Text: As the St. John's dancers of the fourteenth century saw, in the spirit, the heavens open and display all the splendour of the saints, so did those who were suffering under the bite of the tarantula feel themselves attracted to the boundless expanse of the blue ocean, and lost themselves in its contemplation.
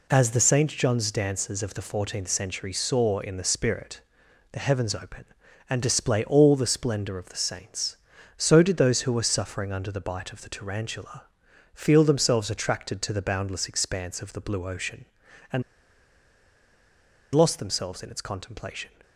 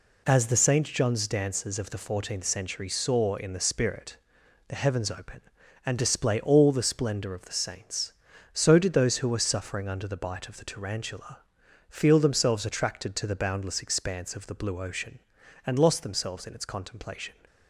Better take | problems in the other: second | pauses between "tarantula" and "feel"; noticeable; at 11.2 s; 0.50 s long; noticeable in the second // pauses between "and" and "lost"; strong; at 15.6 s; 1.7 s long

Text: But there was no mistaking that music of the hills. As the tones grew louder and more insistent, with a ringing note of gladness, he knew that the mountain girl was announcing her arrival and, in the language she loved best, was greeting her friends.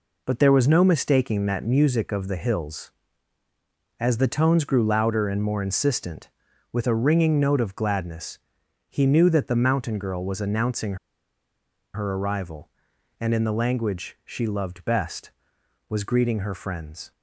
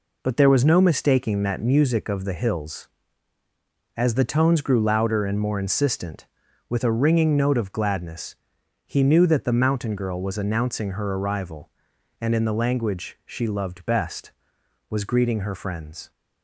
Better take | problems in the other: second | pauses between "announcing" and "her"; at 10.9 s; 0.98 s long

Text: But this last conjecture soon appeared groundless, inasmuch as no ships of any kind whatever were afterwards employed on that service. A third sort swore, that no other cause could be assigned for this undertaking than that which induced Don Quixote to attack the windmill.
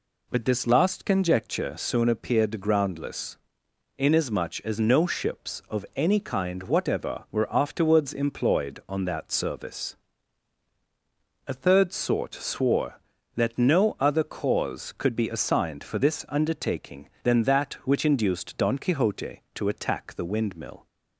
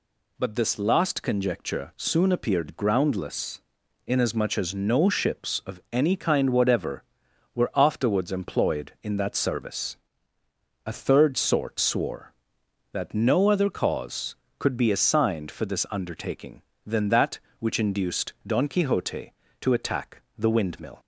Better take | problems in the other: first | says "in" for "on"; at 9.0 s // pauses between "attack" and "the"; slight; at 20.2 s; 0.16 s long

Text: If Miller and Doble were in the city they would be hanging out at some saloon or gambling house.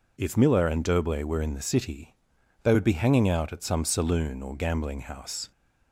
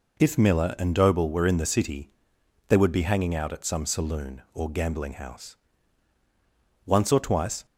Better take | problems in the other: first | pauses between "city" and "they"; noticeable; at 2.0 s; 0.60 s long; noticeable in the first // goes on to say "Once or twice"; noticeable; from 6.8 s on; 0.78 s long

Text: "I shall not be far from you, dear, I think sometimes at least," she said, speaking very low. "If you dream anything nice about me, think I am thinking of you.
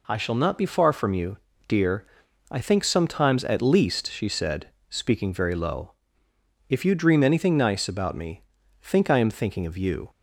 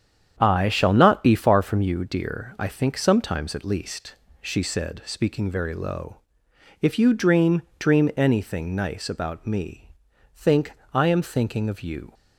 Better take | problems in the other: first | starts louder than the rest; strong; until 1.4 s; 8.5 dB // says "dream" twice; at 7.7 s // pauses between "think" and "I"; slight; at 10.7 s; 0.20 s long

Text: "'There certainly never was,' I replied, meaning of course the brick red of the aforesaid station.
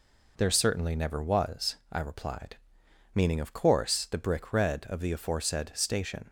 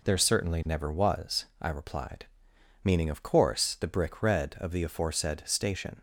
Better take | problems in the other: neither | none

